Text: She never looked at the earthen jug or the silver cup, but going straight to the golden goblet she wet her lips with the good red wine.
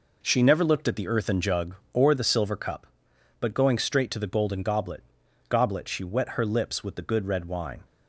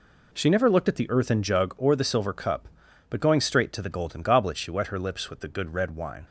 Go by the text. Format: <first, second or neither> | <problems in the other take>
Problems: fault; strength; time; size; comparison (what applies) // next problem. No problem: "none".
second | says "goblet" twice; at 5.4 s